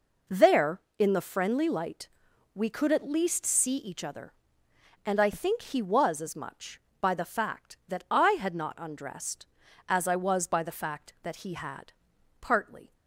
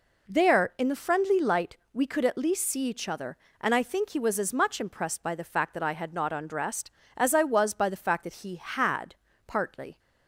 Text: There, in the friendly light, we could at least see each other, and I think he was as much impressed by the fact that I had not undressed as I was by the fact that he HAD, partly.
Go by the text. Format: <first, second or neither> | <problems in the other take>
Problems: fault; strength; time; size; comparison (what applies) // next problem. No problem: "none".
second | skips "impressed"; at 6.9 s